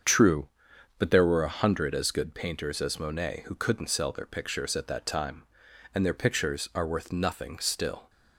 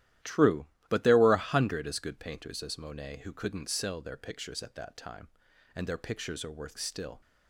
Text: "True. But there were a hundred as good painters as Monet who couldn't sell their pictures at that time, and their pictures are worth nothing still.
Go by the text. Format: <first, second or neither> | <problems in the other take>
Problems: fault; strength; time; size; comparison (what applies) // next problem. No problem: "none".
first | starts louder than the rest; strong; until 1.4 s; 13.5 dB; also in the first // skips "nothing"; at 6.7 s